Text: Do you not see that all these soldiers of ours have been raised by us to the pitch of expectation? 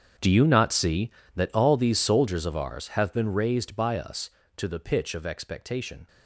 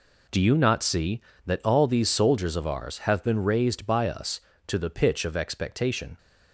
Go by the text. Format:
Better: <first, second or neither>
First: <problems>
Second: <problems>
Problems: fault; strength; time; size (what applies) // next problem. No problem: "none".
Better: second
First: gets quieter; strong; throughout; 16 dB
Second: none